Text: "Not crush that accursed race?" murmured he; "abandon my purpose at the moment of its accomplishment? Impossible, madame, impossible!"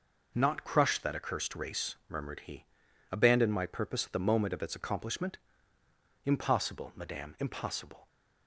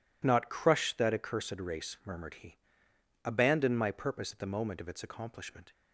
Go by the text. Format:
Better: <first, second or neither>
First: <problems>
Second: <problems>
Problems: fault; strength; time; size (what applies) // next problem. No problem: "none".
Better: first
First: none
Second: stops before "Impossible madame impossible"; at 5.7 s